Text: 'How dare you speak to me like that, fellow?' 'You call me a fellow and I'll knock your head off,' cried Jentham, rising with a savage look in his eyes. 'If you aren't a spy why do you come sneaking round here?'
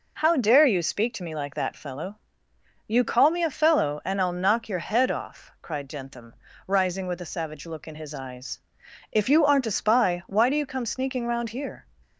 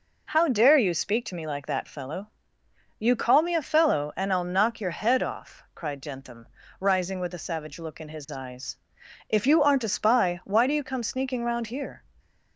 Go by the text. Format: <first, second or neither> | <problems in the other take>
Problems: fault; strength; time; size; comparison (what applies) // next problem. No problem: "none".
neither | none